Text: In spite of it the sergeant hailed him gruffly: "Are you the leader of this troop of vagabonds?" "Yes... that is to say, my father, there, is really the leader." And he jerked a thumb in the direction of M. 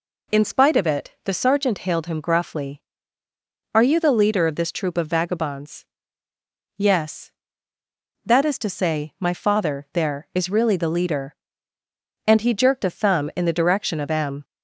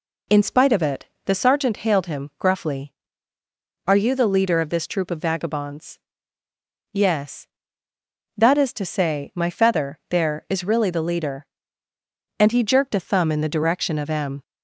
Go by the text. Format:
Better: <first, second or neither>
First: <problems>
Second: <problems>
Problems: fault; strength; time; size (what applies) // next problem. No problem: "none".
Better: first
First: none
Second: pauses between "it" and "the"; slight; at 1.0 s; 0.18 s long // says "feather" for "father"; at 9.4 s